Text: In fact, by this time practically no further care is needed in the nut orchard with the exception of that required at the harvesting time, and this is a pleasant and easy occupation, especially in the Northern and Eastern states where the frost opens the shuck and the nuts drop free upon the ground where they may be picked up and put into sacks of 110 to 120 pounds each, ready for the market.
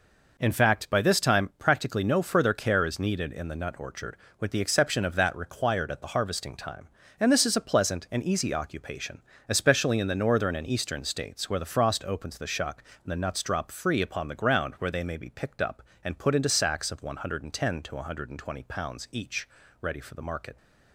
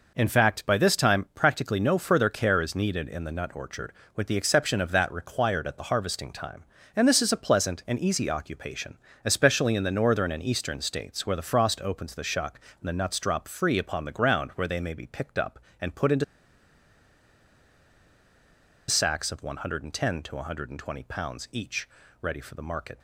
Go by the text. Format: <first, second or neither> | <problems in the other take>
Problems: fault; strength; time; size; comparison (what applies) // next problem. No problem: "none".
first | pauses between "into" and "sacks"; strong; at 16.2 s; 2.6 s long